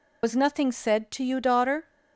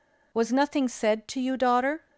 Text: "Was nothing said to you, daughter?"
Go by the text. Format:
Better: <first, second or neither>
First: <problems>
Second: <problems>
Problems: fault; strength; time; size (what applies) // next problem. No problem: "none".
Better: second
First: loses the start of "Was"; at 0.2 s; 60 ms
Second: none